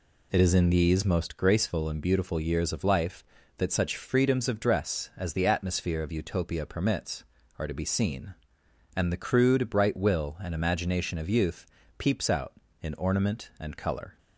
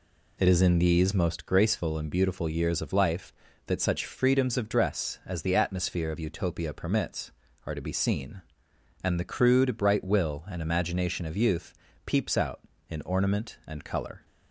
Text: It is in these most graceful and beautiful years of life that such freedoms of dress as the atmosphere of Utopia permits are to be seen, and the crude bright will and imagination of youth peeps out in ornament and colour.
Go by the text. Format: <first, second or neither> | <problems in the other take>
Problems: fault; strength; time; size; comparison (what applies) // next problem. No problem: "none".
neither | pauses between "youth" and "peeps"; slight; the same in both